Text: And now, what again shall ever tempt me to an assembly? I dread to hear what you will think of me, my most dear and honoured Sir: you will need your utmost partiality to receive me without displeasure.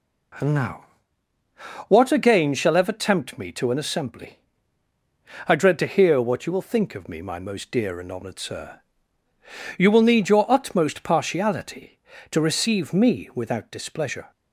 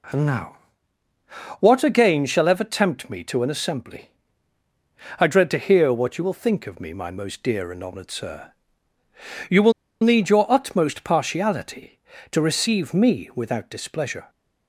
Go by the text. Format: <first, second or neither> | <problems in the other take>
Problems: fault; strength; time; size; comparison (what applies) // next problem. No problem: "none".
first | pauses between "will" and "need"; slight; at 9.7 s; 0.29 s long